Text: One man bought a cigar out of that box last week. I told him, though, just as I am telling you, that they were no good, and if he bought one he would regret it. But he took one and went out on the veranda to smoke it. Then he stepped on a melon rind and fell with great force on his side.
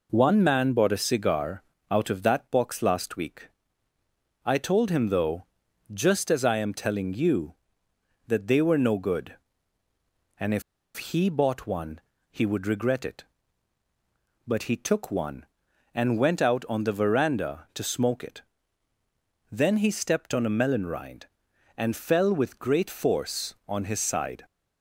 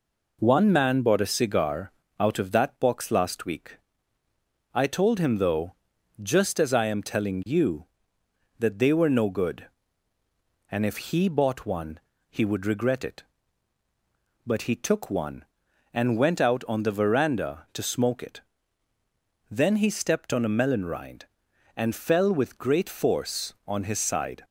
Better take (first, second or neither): second